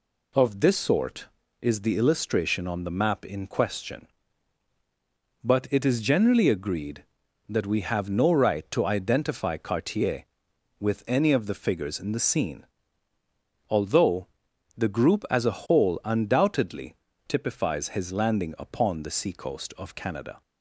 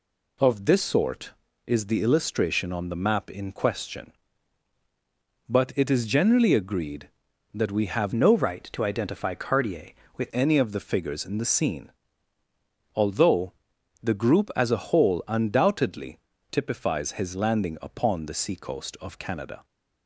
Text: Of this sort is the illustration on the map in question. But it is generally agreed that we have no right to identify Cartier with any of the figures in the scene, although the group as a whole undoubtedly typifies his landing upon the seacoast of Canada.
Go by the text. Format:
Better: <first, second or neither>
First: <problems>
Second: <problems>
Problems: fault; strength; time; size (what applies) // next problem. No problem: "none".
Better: first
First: pauses between "although" and "the"; noticeable; at 14.2 s; 0.50 s long // pauses between "undoubtedly" and "typifies"; slight; at 16.9 s; 0.32 s long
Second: changes voice from "no" to "with"; from 8.1 to 10.3 s; 2.2 s long // pauses between "although" and "the"; noticeable; at 13.5 s; 0.50 s long // pauses between "undoubtedly" and "typifies"; slight; at 16.1 s; 0.32 s long